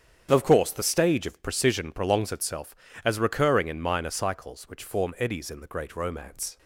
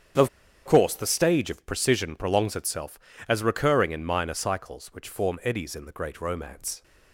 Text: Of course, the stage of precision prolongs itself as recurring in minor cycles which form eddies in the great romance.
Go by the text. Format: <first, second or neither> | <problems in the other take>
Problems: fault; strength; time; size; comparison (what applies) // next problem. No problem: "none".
first | starts louder than the rest; strong; until 1.5 s; 8.5 dB; strong in the first // pauses between "Of" and "course"; at 0.2 s; 0.37 s long